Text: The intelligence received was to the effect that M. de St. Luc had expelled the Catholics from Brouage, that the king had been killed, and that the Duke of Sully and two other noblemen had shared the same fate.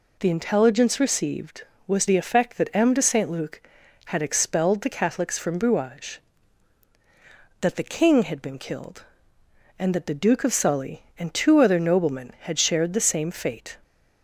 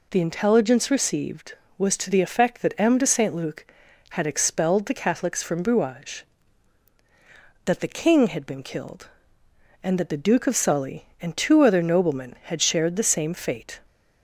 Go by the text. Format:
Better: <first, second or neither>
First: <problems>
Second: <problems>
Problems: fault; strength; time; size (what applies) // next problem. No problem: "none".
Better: second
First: skips "to"; at 2.0 s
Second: none